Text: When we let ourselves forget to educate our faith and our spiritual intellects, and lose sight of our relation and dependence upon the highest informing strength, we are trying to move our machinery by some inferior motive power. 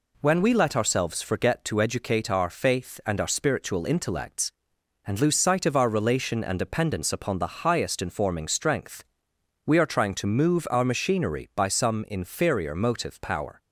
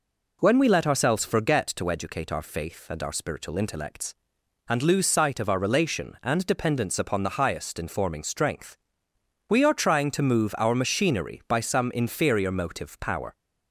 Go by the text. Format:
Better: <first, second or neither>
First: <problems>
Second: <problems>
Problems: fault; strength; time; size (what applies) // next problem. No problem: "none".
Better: neither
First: none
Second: none